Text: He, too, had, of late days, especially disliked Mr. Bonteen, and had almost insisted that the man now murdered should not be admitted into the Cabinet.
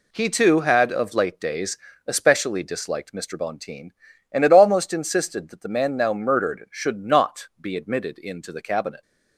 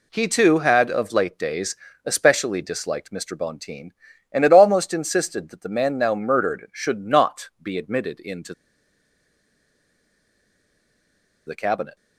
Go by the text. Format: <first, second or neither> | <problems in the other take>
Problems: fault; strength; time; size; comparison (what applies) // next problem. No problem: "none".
first | pauses between "into" and "the"; strong; at 8.5 s; 2.9 s long